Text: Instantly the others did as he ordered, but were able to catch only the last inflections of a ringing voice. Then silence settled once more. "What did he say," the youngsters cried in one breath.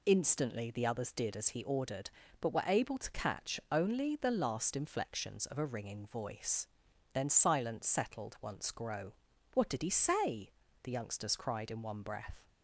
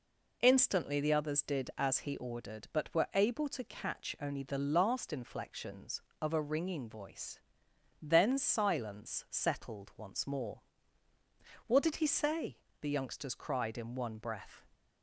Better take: second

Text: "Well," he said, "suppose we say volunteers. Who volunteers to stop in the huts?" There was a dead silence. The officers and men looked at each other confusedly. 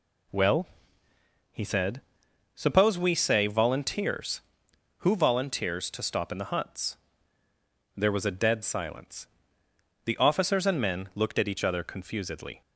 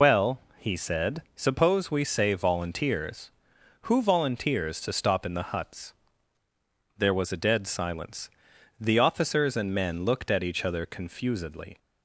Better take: first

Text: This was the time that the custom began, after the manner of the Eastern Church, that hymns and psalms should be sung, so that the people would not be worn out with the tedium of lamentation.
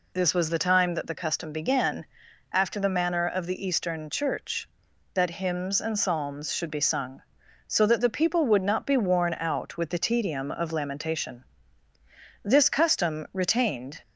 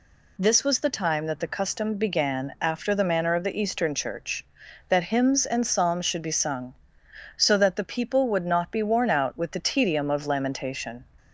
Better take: second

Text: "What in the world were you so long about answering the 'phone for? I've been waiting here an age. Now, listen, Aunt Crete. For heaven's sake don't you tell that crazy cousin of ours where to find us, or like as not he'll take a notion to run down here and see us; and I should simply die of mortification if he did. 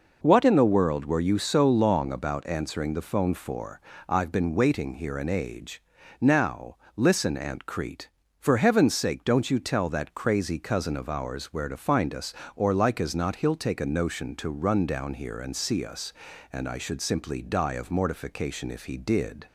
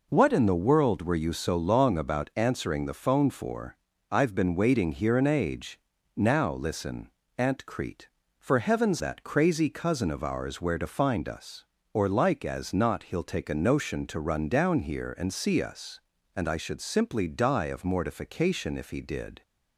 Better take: first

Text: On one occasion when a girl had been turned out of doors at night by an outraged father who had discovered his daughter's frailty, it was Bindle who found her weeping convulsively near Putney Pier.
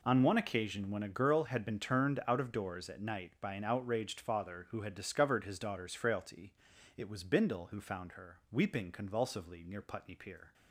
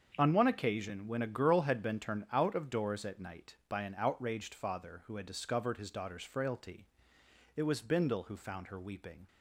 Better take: first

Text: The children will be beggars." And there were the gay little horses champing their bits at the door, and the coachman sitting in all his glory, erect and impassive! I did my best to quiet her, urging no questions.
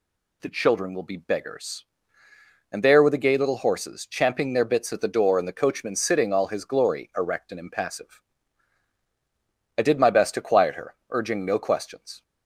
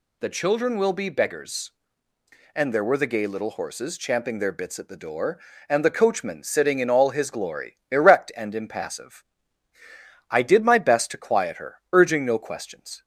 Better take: second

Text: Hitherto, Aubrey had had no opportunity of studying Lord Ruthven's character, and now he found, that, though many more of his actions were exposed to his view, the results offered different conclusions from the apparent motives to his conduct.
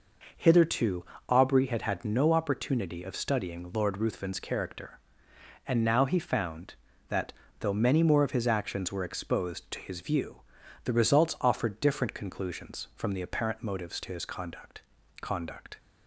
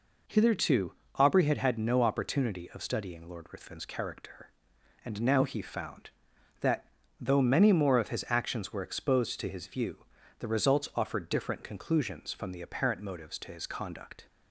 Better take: second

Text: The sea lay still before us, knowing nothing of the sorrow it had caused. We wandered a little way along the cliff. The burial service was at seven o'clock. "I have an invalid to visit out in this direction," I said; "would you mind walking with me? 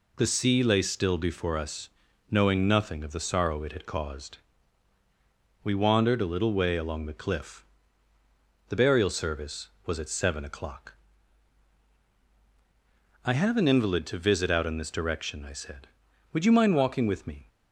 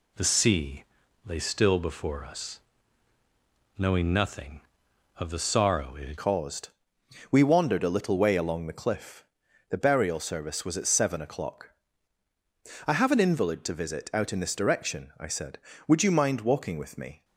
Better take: first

